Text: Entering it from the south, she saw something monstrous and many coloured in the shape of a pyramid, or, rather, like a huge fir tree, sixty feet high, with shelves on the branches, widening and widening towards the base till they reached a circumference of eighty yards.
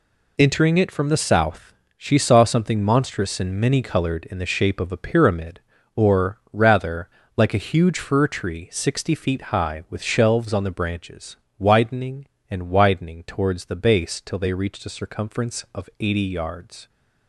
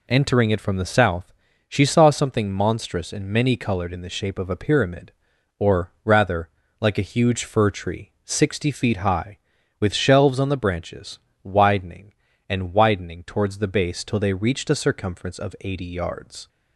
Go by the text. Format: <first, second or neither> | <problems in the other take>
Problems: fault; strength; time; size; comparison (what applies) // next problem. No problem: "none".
neither | none